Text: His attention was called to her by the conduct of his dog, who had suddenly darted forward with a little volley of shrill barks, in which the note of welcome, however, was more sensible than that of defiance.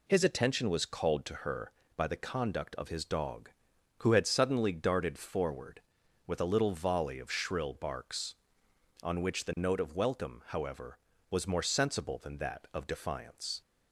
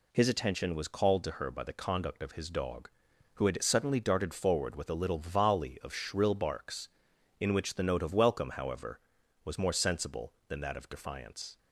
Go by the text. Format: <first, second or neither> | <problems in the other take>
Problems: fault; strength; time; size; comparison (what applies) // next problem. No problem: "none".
second | says "on" for "in"; at 9.0 s